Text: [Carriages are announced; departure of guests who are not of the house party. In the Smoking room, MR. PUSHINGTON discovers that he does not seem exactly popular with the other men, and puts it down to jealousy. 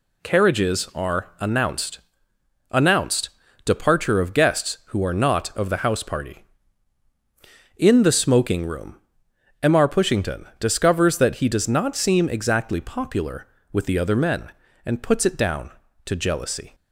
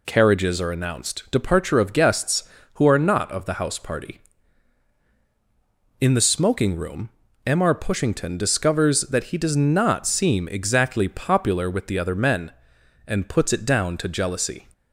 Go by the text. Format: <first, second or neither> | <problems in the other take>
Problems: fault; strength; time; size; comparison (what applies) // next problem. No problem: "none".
second | says "announced" twice; at 2.7 s